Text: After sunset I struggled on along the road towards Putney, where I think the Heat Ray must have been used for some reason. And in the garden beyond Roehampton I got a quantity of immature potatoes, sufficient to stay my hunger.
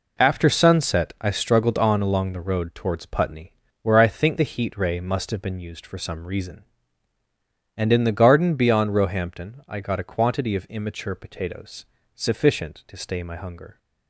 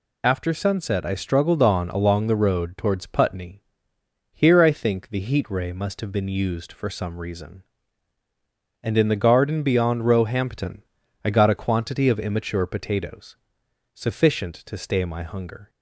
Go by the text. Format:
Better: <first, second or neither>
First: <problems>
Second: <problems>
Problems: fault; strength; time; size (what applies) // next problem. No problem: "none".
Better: first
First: none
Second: says "here" for "where"; at 4.3 s // pauses between "Roehampton" and "I"; at 10.8 s; 0.42 s long